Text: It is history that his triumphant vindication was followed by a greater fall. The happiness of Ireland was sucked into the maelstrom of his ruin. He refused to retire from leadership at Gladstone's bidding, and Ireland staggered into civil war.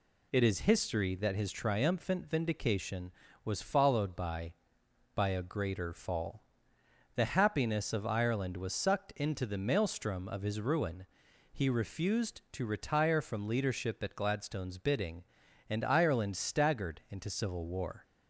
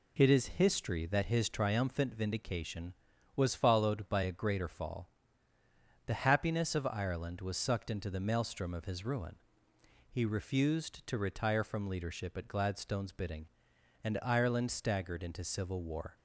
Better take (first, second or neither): second